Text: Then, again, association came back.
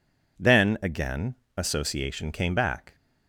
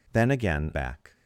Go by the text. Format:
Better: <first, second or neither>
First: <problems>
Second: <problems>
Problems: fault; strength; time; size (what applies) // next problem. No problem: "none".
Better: first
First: none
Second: skips "association came"; at 0.7 s